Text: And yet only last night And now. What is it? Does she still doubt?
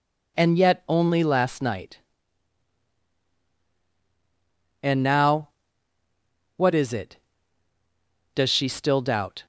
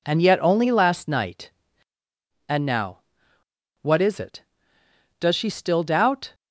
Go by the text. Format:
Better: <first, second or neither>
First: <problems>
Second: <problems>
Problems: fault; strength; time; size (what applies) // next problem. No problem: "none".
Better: neither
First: none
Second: none